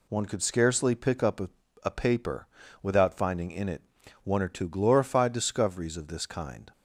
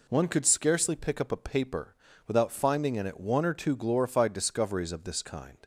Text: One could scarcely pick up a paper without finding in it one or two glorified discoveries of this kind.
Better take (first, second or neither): second